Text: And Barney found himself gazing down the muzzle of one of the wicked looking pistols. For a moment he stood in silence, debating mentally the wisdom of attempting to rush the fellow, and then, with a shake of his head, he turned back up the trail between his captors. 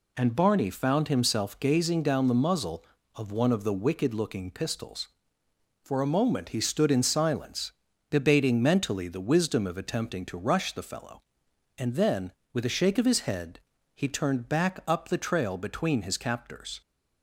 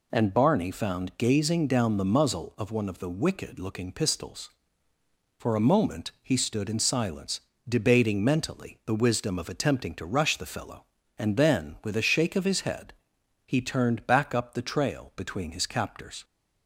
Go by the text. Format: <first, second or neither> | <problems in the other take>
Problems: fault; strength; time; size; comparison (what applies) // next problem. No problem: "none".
first | skips "himself"; at 1.1 s